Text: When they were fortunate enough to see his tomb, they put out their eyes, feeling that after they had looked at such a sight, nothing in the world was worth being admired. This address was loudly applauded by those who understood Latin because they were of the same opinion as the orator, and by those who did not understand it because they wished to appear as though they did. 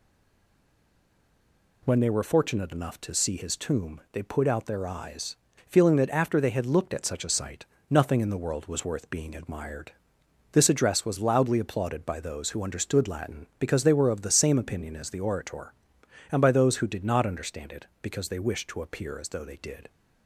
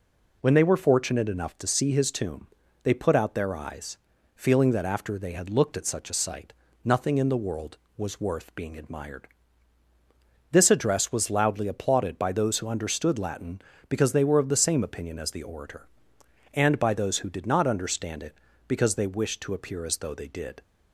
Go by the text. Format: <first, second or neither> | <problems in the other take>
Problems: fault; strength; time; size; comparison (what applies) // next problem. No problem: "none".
second | stays silent before the first word; noticeable; until 1.8 s; 1.8 s long